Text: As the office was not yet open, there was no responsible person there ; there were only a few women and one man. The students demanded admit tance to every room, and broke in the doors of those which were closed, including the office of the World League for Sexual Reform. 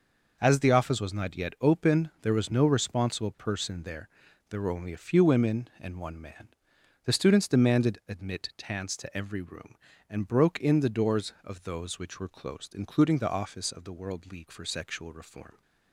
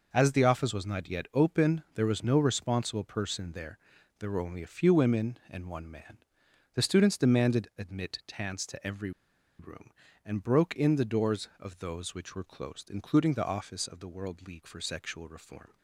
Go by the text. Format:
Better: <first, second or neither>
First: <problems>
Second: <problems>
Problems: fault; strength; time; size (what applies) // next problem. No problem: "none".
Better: first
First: none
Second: pauses between "every" and "room"; noticeable; at 9.1 s; 0.48 s long